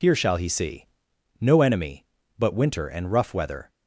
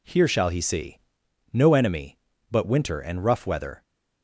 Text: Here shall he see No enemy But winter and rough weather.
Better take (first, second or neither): second